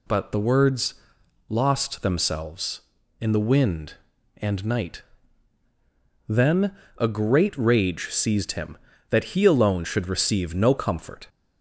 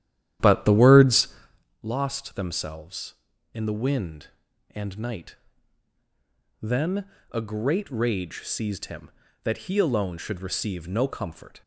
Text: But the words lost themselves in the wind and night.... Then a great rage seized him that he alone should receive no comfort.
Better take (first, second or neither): first